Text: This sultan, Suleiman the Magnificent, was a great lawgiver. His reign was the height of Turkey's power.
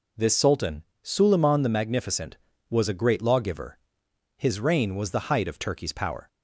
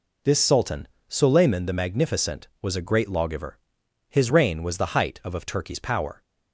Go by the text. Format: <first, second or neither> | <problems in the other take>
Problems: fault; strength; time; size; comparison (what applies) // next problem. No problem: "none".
first | says "of" twice; at 5.3 s